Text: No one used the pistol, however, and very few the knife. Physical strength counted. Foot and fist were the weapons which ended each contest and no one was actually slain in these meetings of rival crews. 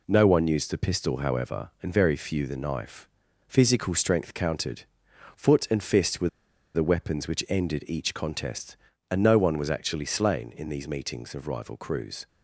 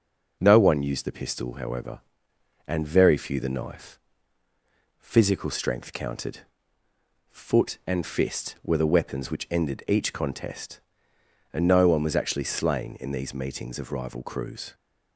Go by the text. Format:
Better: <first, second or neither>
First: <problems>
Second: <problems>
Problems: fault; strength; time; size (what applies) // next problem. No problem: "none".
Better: second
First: pauses between "were" and "the"; noticeable; at 6.2 s; 0.46 s long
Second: none